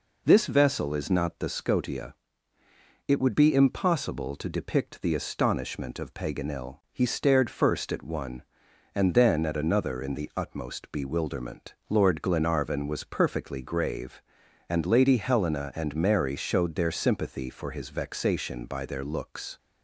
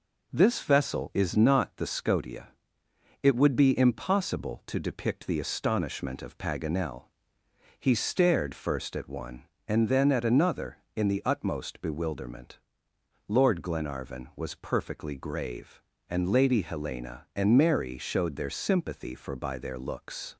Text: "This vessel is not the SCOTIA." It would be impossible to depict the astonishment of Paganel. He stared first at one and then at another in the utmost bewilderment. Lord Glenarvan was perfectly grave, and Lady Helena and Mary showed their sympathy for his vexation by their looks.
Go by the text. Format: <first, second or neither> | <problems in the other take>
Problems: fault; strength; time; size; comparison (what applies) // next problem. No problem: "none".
first | skips "his vexation"; at 19.3 s